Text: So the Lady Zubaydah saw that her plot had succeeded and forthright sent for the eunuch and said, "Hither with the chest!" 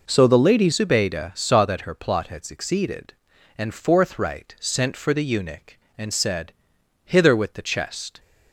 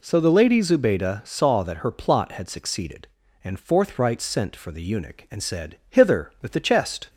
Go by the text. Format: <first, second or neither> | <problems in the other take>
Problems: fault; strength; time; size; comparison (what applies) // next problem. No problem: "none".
second | changes voice at "Zubaydah"; from 0.7 s on; 7.4 s long